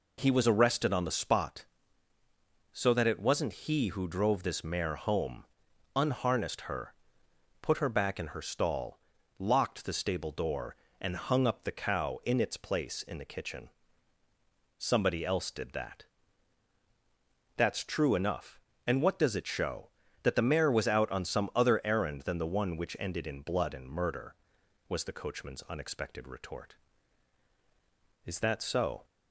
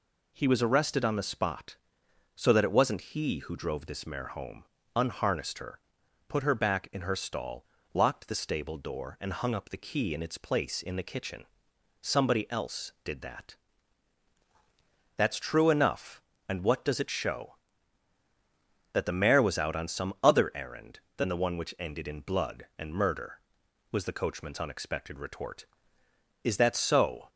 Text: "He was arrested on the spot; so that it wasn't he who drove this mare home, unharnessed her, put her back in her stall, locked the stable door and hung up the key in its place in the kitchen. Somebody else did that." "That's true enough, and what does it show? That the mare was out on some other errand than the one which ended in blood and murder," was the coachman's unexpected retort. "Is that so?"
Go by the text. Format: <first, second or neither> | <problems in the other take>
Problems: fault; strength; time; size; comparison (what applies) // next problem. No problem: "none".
second | says "cow" for "key"; at 11.7 s